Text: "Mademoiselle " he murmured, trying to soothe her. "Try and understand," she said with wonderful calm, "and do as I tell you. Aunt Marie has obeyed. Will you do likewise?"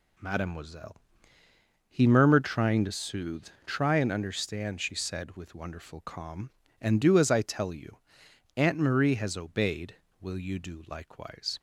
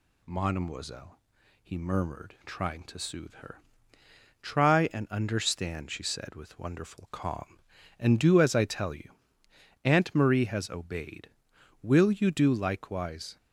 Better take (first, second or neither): second